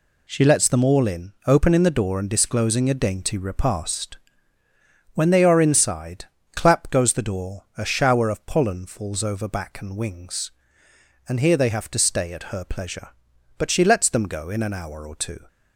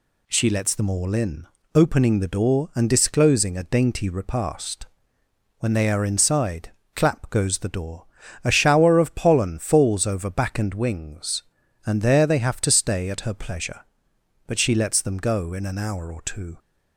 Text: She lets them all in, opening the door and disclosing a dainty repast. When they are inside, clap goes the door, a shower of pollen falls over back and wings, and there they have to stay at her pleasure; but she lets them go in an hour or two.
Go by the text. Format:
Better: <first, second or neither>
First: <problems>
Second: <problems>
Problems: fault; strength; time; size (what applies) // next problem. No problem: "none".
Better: second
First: says "here" for "there"; at 11.3 s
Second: none